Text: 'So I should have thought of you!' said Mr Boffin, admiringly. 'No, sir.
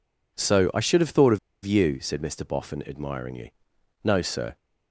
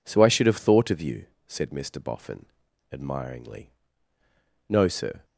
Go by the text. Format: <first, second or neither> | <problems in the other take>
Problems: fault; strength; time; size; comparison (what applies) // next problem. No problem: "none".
second | pauses between "of" and "you"; slight; at 1.3 s; 0.26 s long